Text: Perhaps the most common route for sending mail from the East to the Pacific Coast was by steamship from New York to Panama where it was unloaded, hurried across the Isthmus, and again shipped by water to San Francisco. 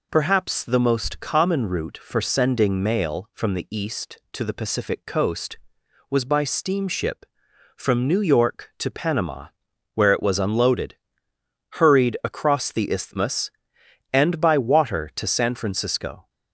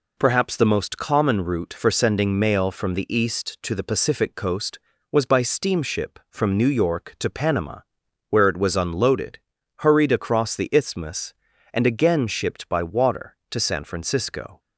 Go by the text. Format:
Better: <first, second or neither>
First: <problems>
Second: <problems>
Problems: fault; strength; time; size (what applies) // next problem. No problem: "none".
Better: second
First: pauses between "Panama" and "where"; noticeable; at 9.4 s; 0.46 s long // skips "again shipped"; at 14.3 s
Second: pauses between "Panama" and "where"; noticeable; at 7.8 s; 0.48 s long